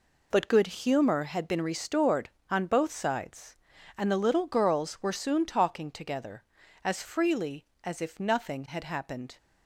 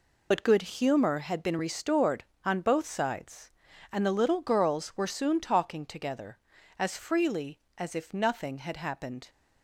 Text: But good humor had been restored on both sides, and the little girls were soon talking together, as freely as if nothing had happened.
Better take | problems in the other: first | loses the start of "But"; at 0.3 s; 40 ms

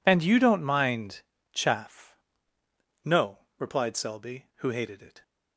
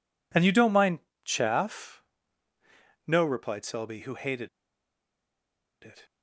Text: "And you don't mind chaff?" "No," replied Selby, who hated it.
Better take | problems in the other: first | pauses between "mind" and "chaff"; slight; at 1.0 s; 0.24 s long; slight in the first // pauses between "hated" and "it"; strong; at 4.4 s; 1.3 s long

